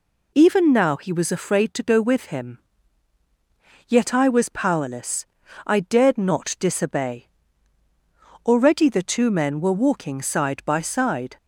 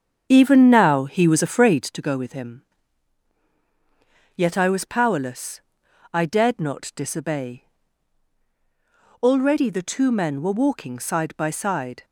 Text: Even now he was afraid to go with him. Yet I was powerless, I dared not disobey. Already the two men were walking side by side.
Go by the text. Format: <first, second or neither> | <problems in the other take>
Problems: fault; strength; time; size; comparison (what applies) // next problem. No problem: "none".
first | starts louder than the rest; strong; until 2.0 s; 7.5 dB